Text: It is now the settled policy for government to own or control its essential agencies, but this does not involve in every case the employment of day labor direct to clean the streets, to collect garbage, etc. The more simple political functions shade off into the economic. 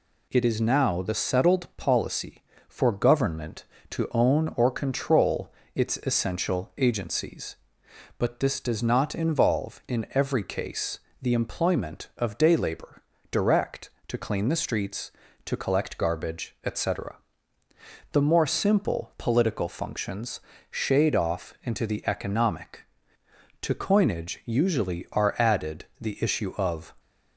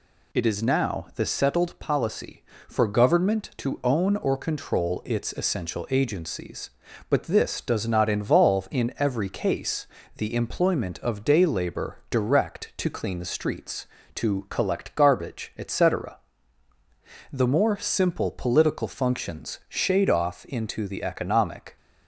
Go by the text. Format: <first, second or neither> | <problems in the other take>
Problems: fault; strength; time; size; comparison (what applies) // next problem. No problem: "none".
second | pauses between "control" and "its"; slight; at 5.5 s; 0.22 s long // pauses between "case" and "the"; slight; at 10.9 s; 0.24 s long; slight in the second // pauses between "labor" and "direct"; slight; at 13.0 s; 0.28 s long // pauses between "functions" and "shade"; slight; at 20.4 s; 0.30 s long // goes on to say "To coinage usually are added the issue of"; strong; from 23.6 s on; 3.3 s long